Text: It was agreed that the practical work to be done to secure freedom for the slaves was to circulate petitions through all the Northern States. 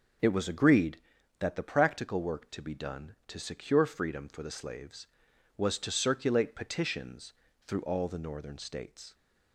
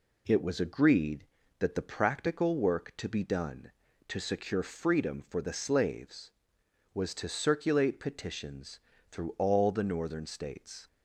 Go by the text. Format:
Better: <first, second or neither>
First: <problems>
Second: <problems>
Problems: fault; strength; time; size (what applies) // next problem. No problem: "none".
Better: neither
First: pauses between "petitions" and "through"; slight; at 7.3 s; 0.32 s long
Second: pauses between "petitions" and "through"; slight; at 8.7 s; 0.32 s long